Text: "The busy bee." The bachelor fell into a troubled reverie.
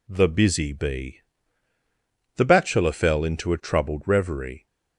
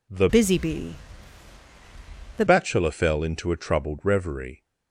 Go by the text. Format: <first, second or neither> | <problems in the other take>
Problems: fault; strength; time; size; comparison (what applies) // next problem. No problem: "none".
first | changes voice from "busy" to "The"; from 0.2 to 2.4 s; 2.2 s long